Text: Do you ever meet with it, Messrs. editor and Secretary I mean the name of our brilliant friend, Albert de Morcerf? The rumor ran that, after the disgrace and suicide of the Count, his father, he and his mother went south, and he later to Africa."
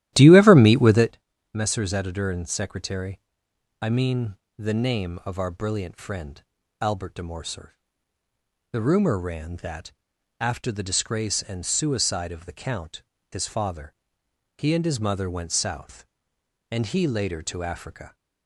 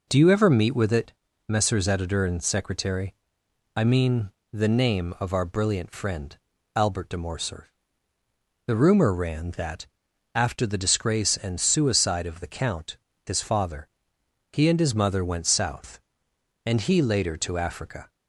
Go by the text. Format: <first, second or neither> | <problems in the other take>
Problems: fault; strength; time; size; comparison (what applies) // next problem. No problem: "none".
second | starts louder than the rest; strong; until 1.1 s; 13.5 dB // pauses between "Secretary" and "I"; noticeable; at 3.1 s; 0.64 s long; noticeable in the second // pauses between "mean" and "the"; slight; at 4.3 s; 0.20 s long; slight in the second